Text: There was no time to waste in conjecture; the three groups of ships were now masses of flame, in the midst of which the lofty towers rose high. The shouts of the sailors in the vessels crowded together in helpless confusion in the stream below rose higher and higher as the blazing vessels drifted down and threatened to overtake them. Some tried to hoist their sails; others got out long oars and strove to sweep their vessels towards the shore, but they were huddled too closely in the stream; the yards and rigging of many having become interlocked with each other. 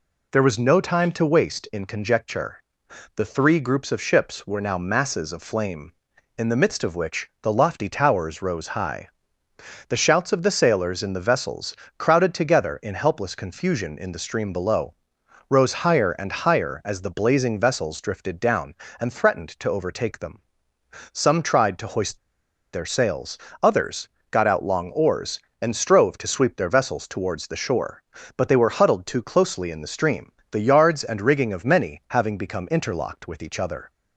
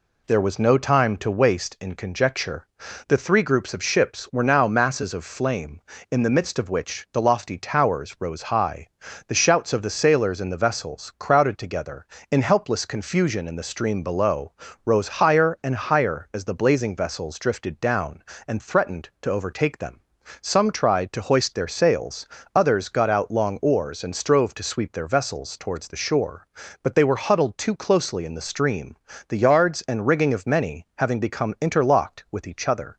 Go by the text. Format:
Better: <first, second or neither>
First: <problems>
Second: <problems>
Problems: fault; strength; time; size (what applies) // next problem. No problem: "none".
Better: second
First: pauses between "vessels" and "crowded"; slight; at 11.7 s; 0.24 s long // pauses between "below" and "rose"; noticeable; at 14.9 s; 0.56 s long // pauses between "hoist" and "their"; noticeable; at 22.1 s; 0.55 s long // pauses between "others" and "got"; slight; at 24.0 s; 0.24 s long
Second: pauses between "below" and "rose"; slight; at 14.5 s; 0.34 s long